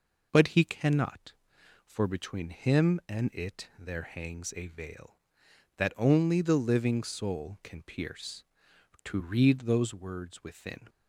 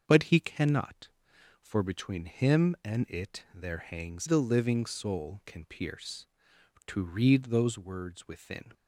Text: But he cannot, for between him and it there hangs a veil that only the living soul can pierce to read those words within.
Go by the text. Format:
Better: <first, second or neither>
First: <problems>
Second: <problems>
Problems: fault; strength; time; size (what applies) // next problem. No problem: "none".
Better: first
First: none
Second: starts louder than the rest; until 1.0 s; 6.5 dB // skips "a veil that only"; at 4.2 s